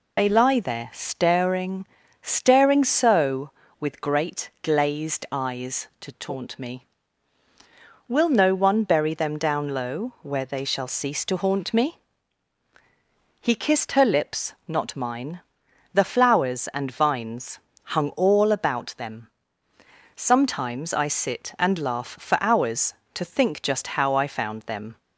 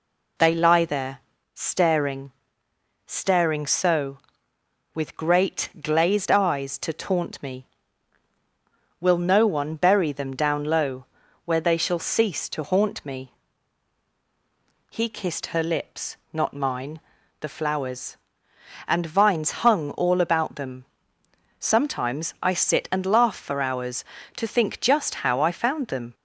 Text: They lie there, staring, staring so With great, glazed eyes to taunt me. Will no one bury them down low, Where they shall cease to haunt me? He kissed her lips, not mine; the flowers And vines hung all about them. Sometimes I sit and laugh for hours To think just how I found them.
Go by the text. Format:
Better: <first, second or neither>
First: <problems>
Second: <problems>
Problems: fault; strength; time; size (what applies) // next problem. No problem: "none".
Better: second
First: loses the start of "They"; at 0.1 s; 55 ms // pauses between "vines" and "hung"; slight; at 17.5 s; 0.24 s long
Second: none